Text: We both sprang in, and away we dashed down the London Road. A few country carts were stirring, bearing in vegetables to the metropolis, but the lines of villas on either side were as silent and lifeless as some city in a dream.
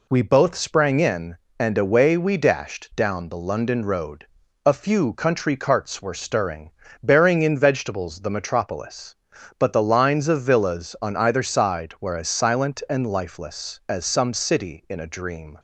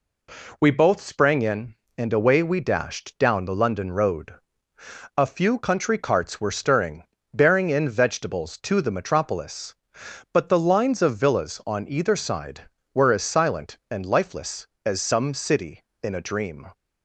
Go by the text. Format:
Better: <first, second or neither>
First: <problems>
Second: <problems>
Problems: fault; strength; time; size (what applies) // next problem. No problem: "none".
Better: second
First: skips "to"; at 8.2 s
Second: none